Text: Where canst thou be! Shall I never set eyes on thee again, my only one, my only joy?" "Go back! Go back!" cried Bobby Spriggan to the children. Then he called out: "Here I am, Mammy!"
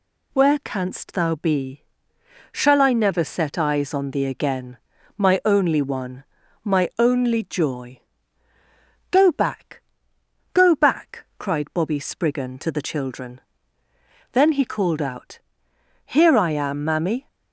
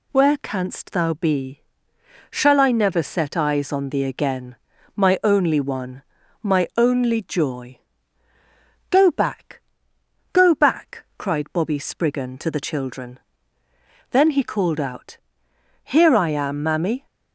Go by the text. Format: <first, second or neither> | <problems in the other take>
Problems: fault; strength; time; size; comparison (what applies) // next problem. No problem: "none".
neither | none